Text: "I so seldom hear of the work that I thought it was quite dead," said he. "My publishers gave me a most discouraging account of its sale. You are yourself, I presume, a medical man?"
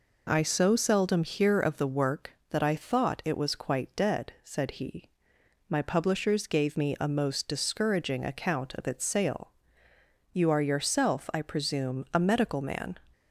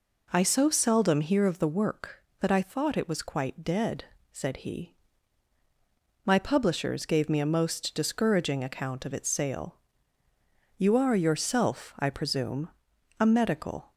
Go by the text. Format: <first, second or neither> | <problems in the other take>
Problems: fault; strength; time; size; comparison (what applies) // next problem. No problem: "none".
first | stops before "man"; at 13.9 s